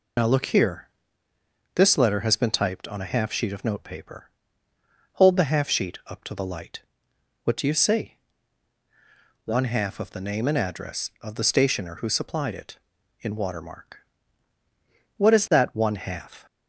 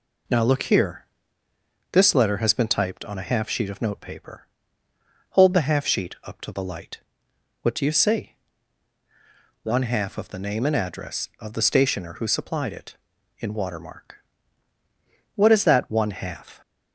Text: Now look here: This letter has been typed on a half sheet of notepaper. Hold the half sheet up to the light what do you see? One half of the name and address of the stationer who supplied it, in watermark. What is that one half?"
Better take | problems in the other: second | loses the start of "Now"; at 0.1 s; 65 ms // pauses between "light" and "what"; noticeable; at 6.8 s; 0.64 s long; noticeable in the second

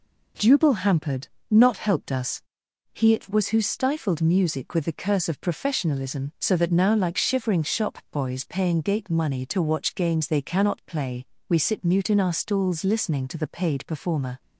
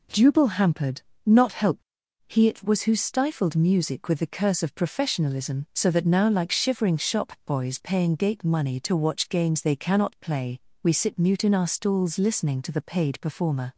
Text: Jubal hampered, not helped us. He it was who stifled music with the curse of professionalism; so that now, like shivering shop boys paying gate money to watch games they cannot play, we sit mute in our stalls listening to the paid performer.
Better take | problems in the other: first | skips "us"; at 2.0 s

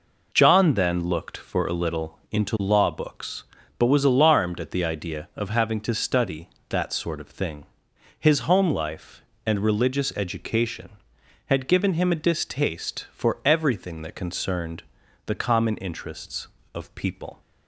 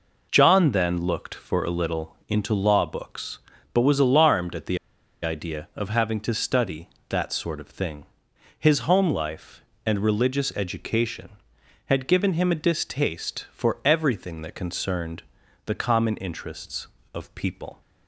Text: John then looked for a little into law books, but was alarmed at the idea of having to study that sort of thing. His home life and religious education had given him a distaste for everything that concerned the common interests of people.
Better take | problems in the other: first | pauses between "the" and "idea"; noticeable; at 4.7 s; 0.46 s long // pauses between "concerned" and "the"; at 15.2 s; 0.44 s long; also in the first

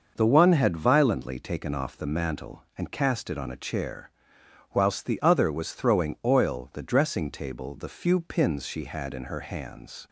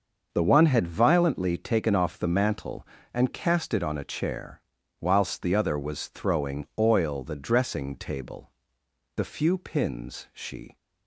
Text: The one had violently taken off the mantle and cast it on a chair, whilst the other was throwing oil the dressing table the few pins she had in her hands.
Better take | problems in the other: first | starts louder than the rest; until 1.3 s; 6.5 dB; noticeable in the first // pauses between "table" and "the"; noticeable; at 8.4 s; 0.66 s long // stops before "had in her hands"; at 10.7 s

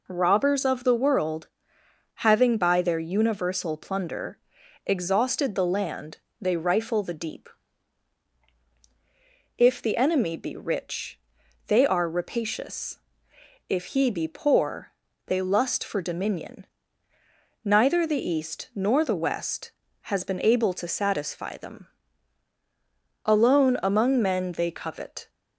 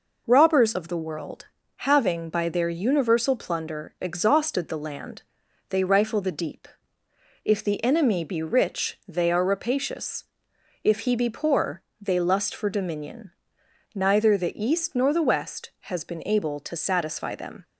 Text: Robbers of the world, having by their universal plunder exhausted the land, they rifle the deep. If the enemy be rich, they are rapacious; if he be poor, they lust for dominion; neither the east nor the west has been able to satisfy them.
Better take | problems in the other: second | pauses between "plunder" and "exhausted"; noticeable; at 4.3 s; 0.48 s long // goes on to say "Alone among men they covet"; strong; from 23.2 s on; 2.0 s long

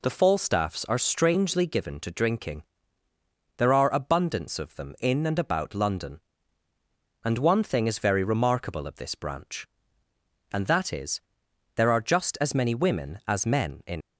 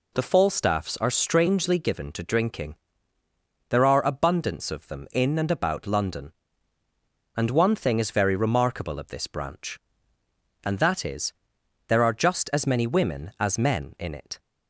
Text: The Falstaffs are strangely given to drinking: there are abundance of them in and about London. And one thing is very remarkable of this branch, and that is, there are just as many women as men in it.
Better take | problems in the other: second | stops before "it"; at 14.0 s

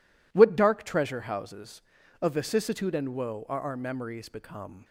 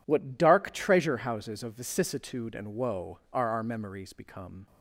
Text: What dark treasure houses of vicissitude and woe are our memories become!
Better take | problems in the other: neither | none

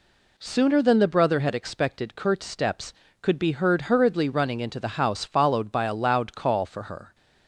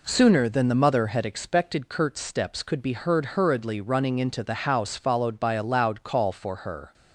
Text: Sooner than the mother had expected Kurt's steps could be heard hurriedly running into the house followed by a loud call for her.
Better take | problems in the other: second | says "brother" for "mother"; at 1.0 s

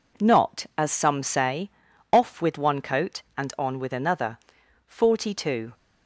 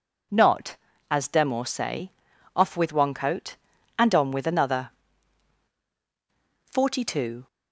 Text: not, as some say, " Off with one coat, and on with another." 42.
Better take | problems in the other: first | says "demor" for "some"; at 1.2 s

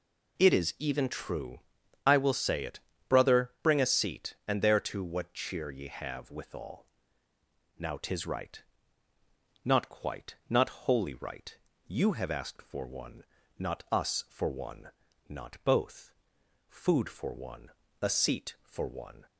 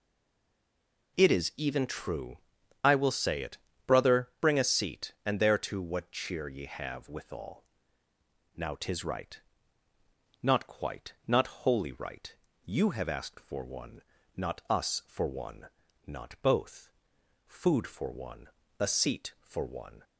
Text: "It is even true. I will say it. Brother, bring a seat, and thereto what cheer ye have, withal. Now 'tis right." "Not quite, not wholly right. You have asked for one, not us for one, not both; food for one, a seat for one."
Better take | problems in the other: first | stays silent before the first word; until 1.1 s; 1.1 s long

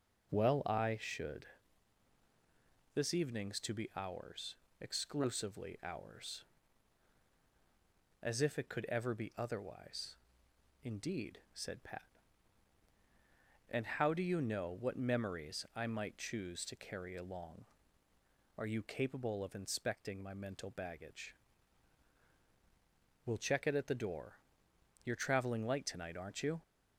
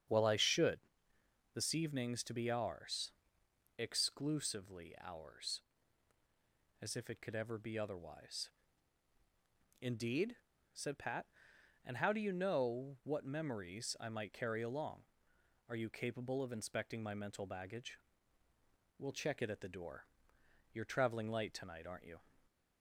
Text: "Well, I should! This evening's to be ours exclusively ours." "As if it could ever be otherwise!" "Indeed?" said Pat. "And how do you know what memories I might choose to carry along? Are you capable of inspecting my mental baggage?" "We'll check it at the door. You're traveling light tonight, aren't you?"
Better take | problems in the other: first | starts louder than the rest; strong; until 1.8 s; 8 dB // pauses between "ours" and "exclusively"; noticeable; at 3.1 s; 0.64 s long; slight in the first // skips "choose to"; at 14.3 s

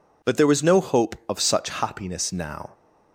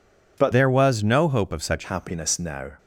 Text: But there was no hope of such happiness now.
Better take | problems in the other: first | changes voice from "there" to "such"; from 0.5 to 1.8 s; 1.3 s long

